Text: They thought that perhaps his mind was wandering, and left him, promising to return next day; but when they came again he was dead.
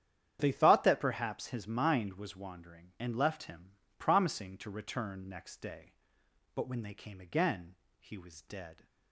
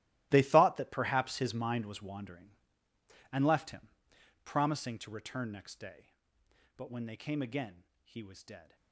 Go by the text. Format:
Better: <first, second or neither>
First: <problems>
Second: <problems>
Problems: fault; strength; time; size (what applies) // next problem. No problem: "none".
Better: first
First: starts louder than the rest; strong; until 1.4 s; 9.5 dB // pauses between "again" and "he"; slight; at 7.7 s; 0.24 s long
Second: gets quieter; strong; throughout; 17 dB // starts louder than the rest; strong; until 1.3 s; 17 dB // pauses between "again" and "he"; slight; at 7.8 s; 0.20 s long